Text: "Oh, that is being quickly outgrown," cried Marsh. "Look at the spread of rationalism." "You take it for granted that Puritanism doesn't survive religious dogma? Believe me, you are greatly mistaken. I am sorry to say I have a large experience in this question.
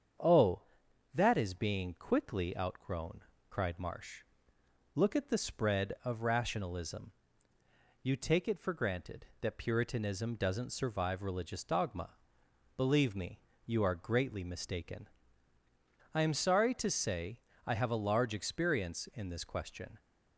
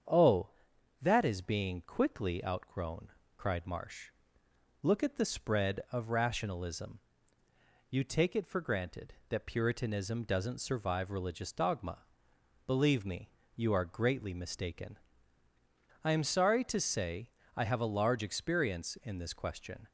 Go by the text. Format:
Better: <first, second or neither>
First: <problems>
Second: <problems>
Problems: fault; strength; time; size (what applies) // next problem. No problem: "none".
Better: neither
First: starts louder than the rest; strong; until 1.7 s; 7.5 dB // pauses between "say" and "I"; slight; at 17.4 s; 0.26 s long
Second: starts louder than the rest; strong; until 1.6 s; 7.5 dB // pauses between "say" and "I"; slight; at 17.3 s; 0.26 s long